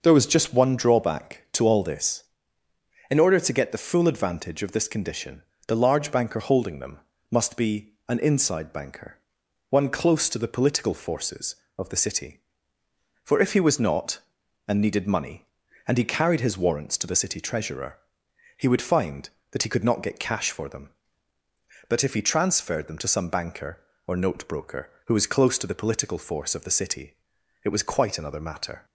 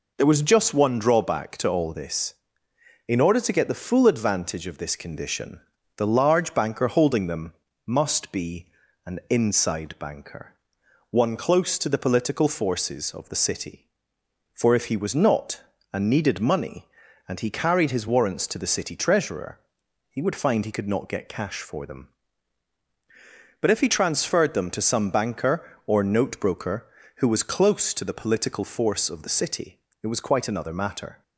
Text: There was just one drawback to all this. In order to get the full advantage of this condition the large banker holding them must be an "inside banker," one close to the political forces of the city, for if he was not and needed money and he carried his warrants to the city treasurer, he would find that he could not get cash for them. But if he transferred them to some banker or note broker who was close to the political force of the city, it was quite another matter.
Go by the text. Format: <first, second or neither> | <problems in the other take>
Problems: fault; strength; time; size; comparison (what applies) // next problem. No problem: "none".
first | pauses between "condition" and "the"; slight; at 5.5 s; 0.36 s long; slight in the first // pauses between "them" and "must"; slight; at 7.5 s; 0.32 s long; slight in the first // pauses between "be" and "an"; at 8.6 s; 0.40 s long; slight in the first // skips "that"; at 20.6 s